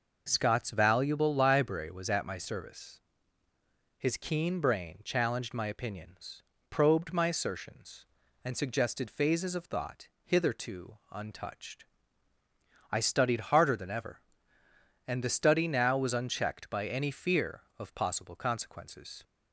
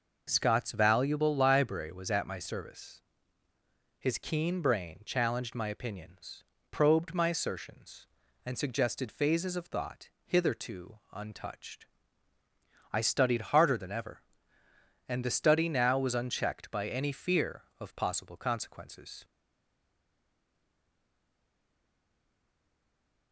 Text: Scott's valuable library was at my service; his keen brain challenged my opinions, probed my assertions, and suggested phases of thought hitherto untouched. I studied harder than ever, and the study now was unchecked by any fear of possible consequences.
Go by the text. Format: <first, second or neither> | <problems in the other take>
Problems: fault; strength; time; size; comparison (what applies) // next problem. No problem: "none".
first | pauses between "thought" and "hitherto"; slight; at 10.1 s; 0.16 s long; slight in the first // pauses between "hitherto" and "untouched"; slight; at 10.9 s; 0.16 s long; slight in the first // stays silent after the last word; strong; from 19.2 s on; 4.1 s long